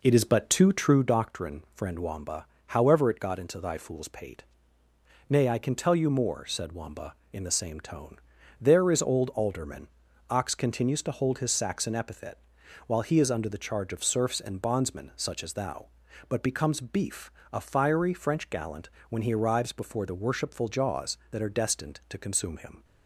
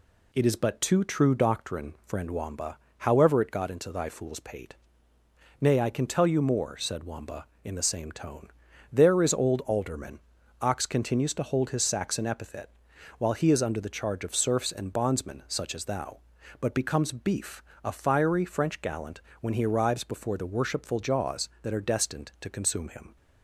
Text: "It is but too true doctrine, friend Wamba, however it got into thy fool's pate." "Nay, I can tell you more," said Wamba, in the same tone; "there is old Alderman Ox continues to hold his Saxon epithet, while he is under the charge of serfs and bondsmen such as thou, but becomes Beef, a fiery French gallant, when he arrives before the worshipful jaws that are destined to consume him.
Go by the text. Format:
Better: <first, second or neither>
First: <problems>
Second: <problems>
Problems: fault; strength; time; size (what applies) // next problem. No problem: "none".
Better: second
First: starts louder than the rest; noticeable; until 1.0 s; 4.5 dB // pauses between "Alderman" and "Ox"; at 9.8 s; 0.42 s long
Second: pauses between "Alderman" and "Ox"; at 10.1 s; 0.42 s long